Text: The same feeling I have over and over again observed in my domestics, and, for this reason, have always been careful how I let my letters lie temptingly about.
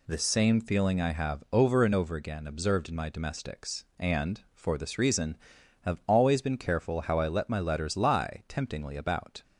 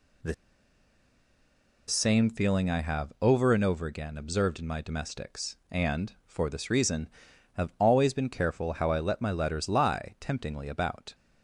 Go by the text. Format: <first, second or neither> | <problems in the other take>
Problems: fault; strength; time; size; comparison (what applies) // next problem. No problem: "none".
first | pauses between "The" and "same"; strong; at 0.3 s; 1.5 s long